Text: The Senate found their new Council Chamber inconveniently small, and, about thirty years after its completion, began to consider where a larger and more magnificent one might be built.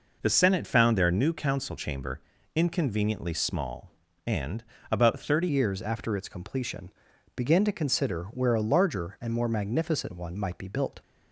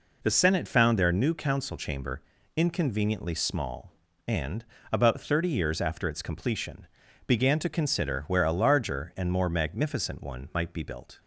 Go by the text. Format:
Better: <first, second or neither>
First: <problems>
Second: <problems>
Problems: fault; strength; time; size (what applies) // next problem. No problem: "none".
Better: second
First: pauses between "Chamber" and "inconveniently"; slight; at 2.2 s; 0.34 s long // changes voice at "years"; from 5.4 s on; 5.6 s long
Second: pauses between "Chamber" and "inconveniently"; slight; at 2.2 s; 0.34 s long